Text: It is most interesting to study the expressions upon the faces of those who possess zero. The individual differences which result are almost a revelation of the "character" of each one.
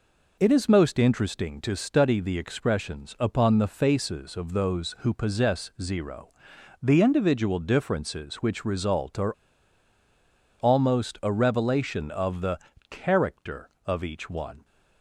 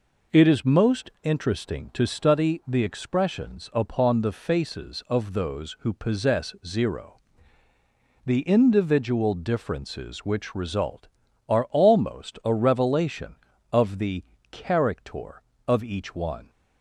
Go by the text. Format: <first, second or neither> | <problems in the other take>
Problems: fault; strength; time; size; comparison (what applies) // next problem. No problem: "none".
second | pauses between "are" and "almost"; strong; at 9.3 s; 1.2 s long // pauses between "the" and "character"; slight; at 12.5 s; 0.32 s long; slight in the second